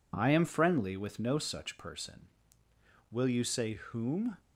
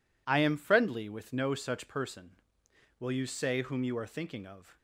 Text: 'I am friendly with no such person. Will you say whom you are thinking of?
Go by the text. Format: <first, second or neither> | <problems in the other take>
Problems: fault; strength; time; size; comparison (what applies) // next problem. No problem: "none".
second | stops before "you are thinking of"; at 4.3 s